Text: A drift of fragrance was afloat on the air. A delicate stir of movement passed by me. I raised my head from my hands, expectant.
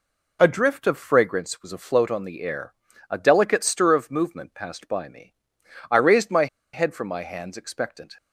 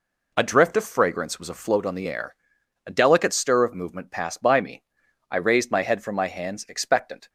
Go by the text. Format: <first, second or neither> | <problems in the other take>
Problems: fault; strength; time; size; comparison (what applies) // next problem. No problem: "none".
second | pauses between "my" and "head"; slight; at 6.4 s; 0.27 s long